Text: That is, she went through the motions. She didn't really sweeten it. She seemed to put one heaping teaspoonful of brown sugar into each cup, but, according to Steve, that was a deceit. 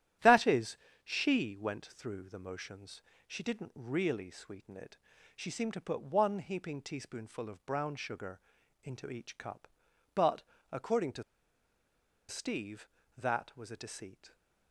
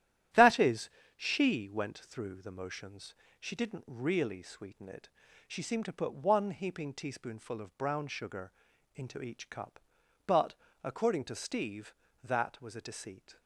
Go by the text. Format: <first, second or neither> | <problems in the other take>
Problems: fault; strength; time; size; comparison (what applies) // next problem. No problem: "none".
second | starts louder than the rest; strong; until 1.4 s; 11.5 dB; strong in the second // pauses between "sugar" and "into"; at 8.3 s; 0.44 s long; also in the second // pauses between "to" and "Steve"; at 11.2 s; 1.0 s long